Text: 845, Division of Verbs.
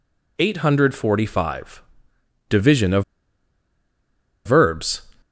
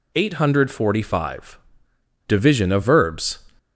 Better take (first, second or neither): second